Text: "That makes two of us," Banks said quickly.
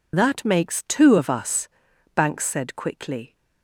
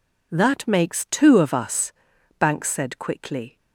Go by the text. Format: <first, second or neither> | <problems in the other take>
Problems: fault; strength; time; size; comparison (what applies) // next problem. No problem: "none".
second | loses the start of "That"; at 0.1 s; 45 ms